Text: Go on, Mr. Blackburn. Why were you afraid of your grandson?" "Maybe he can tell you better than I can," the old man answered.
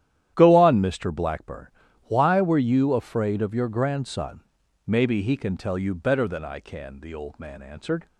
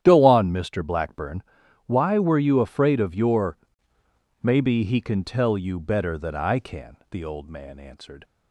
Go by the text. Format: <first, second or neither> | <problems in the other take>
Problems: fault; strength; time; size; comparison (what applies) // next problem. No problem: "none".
first | starts louder than the rest; strong; until 1.0 s; 10.5 dB; strong in the first // skips "grandson"; at 3.9 s